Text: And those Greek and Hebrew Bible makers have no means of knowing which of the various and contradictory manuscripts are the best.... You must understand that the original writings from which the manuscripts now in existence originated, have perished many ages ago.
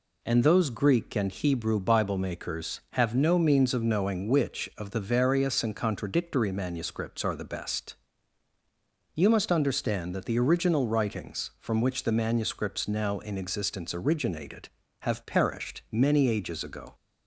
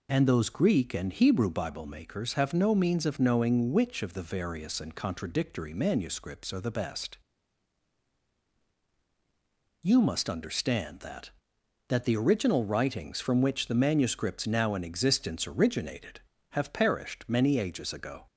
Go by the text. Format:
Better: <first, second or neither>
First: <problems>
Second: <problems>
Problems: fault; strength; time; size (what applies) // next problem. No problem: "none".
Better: first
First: none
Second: says "that" twice; at 11.8 s